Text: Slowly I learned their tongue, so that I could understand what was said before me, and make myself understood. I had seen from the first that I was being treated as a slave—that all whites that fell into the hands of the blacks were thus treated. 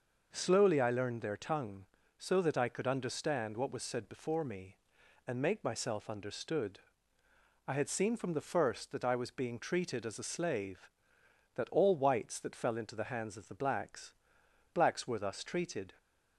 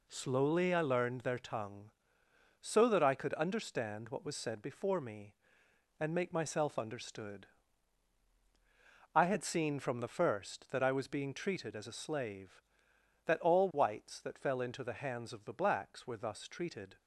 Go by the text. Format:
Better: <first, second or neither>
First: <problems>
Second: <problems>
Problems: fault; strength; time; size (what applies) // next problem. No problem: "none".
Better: second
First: says "blacks" twice; at 14.7 s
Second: none